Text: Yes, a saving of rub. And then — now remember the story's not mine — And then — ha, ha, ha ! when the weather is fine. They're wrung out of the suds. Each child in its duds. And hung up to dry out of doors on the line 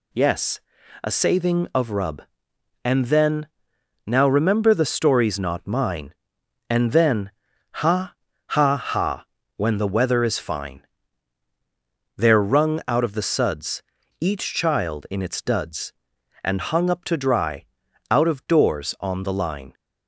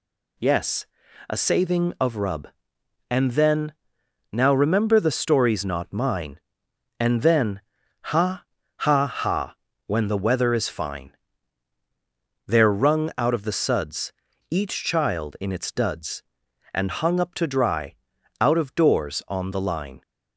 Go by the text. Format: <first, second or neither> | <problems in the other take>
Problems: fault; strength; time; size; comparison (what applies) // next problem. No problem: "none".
neither | pauses between "dry" and "out"; the same in both